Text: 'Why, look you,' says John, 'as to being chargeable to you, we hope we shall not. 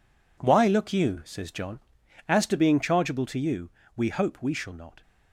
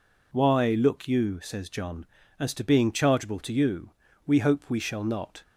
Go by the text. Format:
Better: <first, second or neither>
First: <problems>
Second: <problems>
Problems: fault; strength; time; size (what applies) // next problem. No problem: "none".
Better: neither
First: none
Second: none